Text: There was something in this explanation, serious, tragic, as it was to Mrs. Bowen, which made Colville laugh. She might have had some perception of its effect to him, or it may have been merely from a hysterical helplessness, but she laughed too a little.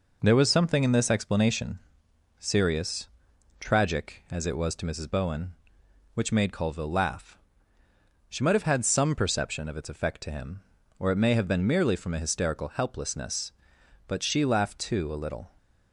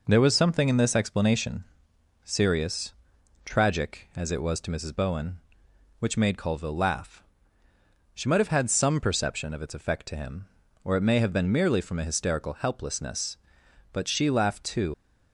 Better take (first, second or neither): first